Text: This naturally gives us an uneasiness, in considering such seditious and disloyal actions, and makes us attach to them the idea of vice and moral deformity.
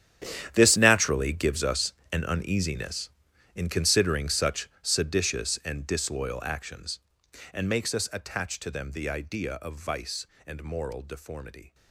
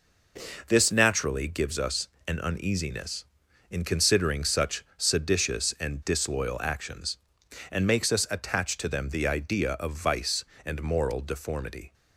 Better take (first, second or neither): second